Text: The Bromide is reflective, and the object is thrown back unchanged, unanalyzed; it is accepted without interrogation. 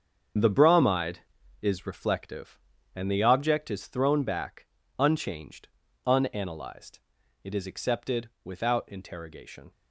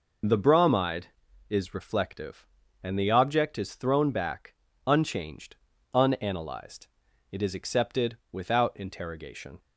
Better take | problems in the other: second | gets quieter; strong; throughout; 10.5 dB // pauses between "back" and "unchanged"; slight; at 4.6 s; 0.32 s long; slight in the second // pauses between "accepted" and "without"; slight; at 8.2 s; 0.16 s long; slight in the second

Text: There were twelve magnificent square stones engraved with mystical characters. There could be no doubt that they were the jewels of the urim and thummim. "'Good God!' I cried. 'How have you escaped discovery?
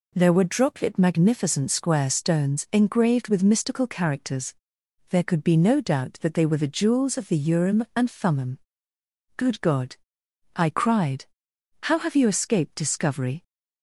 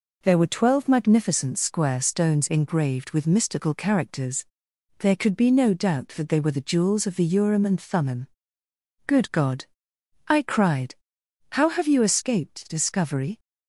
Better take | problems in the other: second | says "droplet" for "twelve"; at 0.4 s

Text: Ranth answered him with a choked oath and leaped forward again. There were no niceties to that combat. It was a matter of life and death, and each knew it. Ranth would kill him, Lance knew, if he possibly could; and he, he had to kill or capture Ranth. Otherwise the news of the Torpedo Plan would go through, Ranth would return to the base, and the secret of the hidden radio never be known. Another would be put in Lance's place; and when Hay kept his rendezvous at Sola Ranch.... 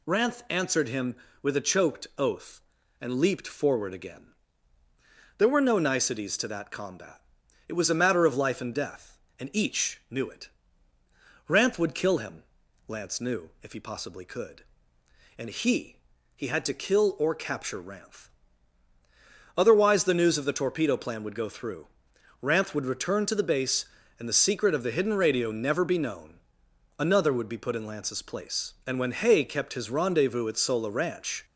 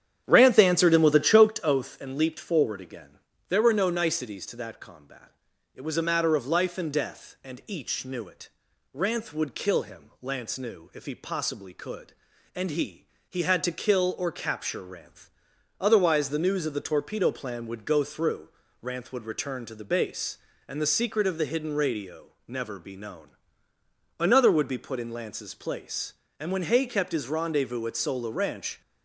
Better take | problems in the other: first | starts louder than the rest; strong; until 1.6 s; 9.5 dB // pauses between "radio" and "never"; slight; at 22.2 s; 0.20 s long

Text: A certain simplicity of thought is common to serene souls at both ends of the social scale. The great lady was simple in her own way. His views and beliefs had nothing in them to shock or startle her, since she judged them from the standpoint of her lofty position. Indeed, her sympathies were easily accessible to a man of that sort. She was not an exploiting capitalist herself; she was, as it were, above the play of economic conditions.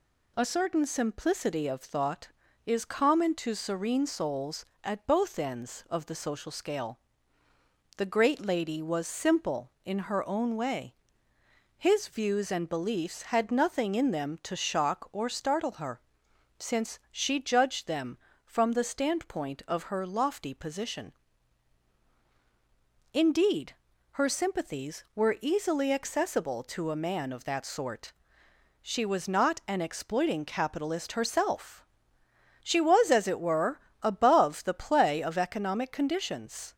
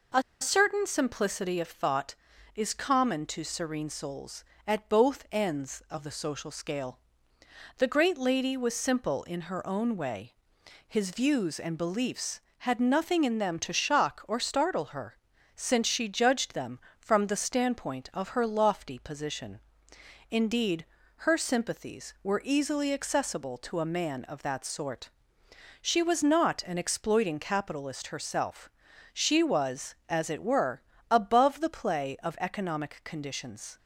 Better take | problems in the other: first | pauses between "A" and "certain"; slight; at 0.2 s; 0.20 s long

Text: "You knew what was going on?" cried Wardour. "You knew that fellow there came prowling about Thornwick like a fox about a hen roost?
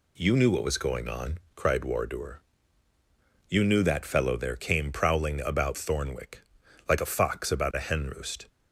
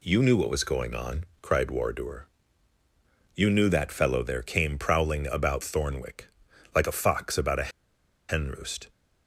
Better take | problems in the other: first | pauses between "Thornwick" and "like"; noticeable; at 6.2 s; 0.48 s long; noticeable in the first // pauses between "a" and "hen"; noticeable; at 7.6 s; 0.60 s long

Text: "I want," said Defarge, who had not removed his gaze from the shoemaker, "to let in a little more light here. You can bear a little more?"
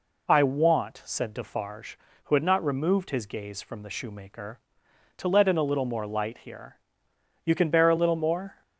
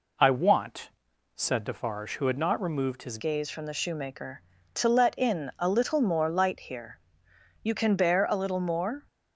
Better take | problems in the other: first | changes voice at "gaze"; from 3.1 s on; 5.9 s long

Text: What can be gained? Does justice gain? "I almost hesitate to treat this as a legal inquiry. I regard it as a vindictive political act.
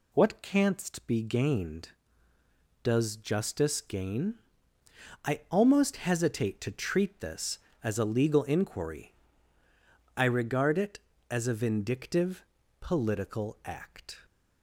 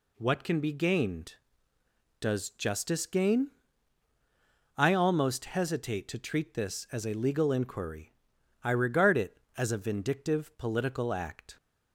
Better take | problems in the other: second | says "canst" for "can"; at 0.4 s // pauses between "vindictive" and "political"; at 12.4 s; 0.38 s long

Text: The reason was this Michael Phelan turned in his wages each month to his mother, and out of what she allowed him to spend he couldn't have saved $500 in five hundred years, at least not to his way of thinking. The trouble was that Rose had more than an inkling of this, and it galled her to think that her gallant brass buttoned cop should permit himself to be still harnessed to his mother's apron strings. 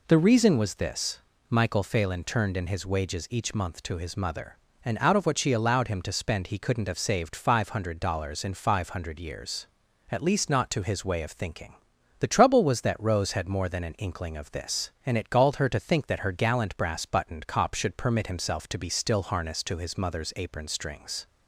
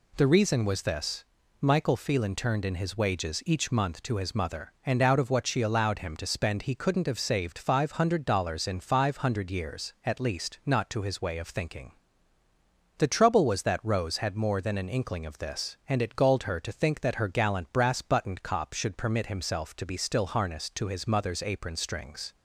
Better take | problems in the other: neither | pauses between "this" and "Michael"; slight; the same in both

